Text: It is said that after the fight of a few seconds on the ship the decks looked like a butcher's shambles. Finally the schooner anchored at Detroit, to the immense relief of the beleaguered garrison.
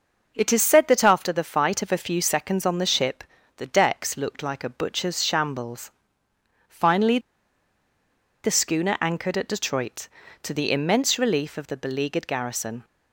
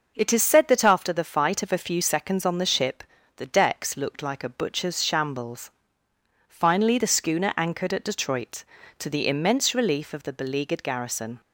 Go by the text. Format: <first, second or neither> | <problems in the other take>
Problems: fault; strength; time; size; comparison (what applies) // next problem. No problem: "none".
second | starts louder than the rest; noticeable; until 1.3 s; 6 dB; noticeable in the second // pauses between "ship" and "the"; slight; at 3.2 s; 0.36 s long; slight in the second // pauses between "Finally" and "the"; at 7.1 s; 1.2 s long